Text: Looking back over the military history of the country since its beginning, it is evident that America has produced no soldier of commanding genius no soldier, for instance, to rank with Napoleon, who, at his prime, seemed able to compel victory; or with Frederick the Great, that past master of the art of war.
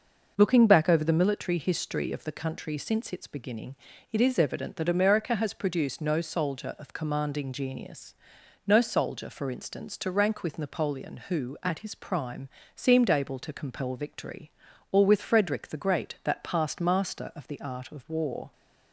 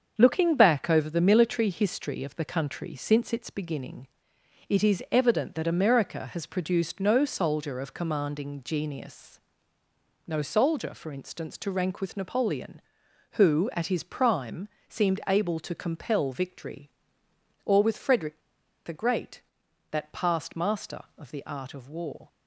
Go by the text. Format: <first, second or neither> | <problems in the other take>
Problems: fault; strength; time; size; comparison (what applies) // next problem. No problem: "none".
first | starts louder than the rest; until 1.2 s; 7 dB // pauses between "genius" and "no"; noticeable; at 9.3 s; 0.86 s long; noticeable in the first // pauses between "Frederick" and "the"; noticeable; at 18.3 s; 0.46 s long